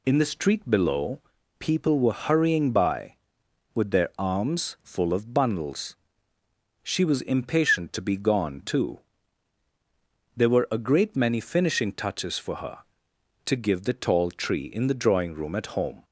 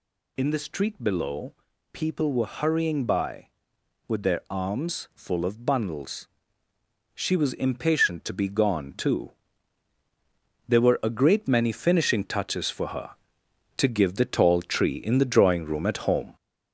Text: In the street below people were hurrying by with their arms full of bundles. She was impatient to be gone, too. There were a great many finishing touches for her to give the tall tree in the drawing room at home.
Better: first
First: pauses between "below" and "people"; at 1.1 s; 0.40 s long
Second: gets louder; throughout; 4 dB // pauses between "below" and "people"; at 1.5 s; 0.40 s long

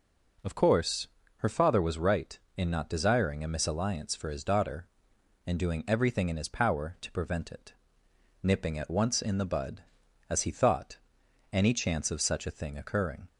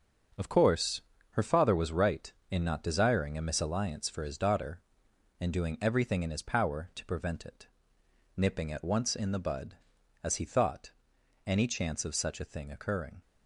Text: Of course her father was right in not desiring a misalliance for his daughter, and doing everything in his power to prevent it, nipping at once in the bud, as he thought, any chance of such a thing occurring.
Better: first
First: pauses between "course" and "her"; slight; at 1.0 s; 0.30 s long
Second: gets quieter; strong; throughout; 8 dB // pauses between "course" and "her"; slight; at 1.0 s; 0.30 s long

